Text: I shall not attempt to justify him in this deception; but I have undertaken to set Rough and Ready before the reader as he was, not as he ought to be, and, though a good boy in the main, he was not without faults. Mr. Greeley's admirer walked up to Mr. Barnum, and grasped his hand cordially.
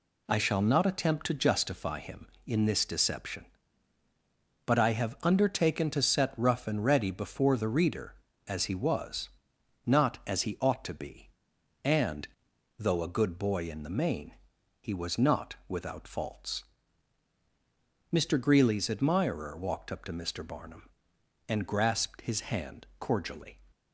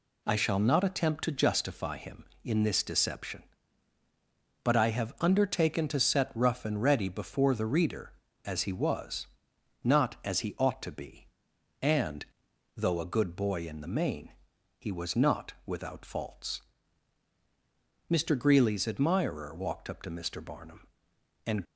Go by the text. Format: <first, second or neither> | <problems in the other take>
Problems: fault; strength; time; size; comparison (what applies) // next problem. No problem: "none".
first | stops before "grasped his hand cordially"; at 21.6 s